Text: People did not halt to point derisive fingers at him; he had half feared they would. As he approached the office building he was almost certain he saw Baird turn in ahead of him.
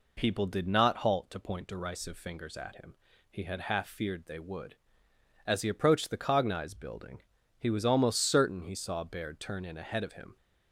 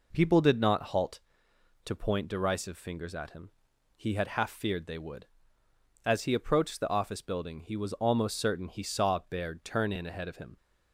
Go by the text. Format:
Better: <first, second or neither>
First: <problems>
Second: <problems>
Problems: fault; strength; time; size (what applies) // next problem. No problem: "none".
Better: second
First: says "cognize" for "office"; at 6.1 s // pauses between "building" and "he"; slight; at 7.1 s; 0.36 s long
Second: none